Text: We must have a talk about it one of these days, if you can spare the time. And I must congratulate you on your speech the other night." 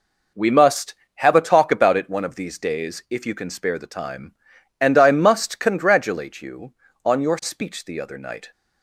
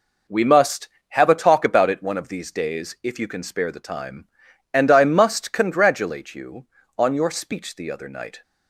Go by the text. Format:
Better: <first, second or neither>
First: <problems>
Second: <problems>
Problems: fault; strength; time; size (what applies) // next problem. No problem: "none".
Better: neither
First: none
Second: none